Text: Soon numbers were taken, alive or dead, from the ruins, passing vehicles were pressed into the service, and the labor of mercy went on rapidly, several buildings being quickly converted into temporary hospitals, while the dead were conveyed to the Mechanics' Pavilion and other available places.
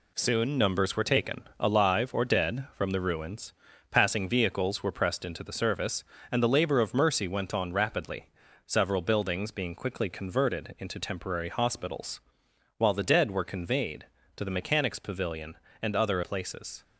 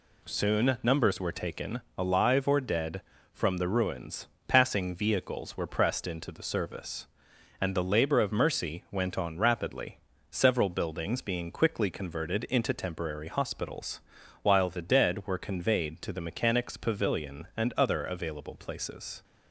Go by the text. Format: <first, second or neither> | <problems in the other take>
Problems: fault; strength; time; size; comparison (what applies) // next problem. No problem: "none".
second | skips "available"; at 16.2 s